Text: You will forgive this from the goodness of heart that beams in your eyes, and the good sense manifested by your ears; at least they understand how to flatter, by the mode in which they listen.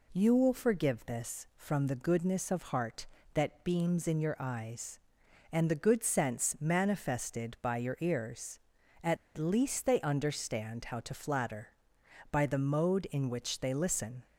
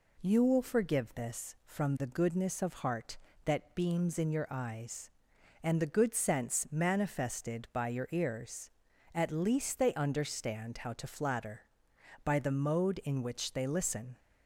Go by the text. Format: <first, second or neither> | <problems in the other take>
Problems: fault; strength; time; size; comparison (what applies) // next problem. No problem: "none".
second | pauses between "at" and "least"; slight; at 9.1 s; 0.20 s long